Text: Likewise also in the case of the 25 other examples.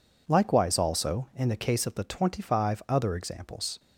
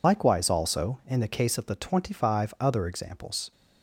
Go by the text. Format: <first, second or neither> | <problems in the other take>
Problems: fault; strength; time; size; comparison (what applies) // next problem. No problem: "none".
first | loses the start of "Likewise"; at 0.0 s; 50 ms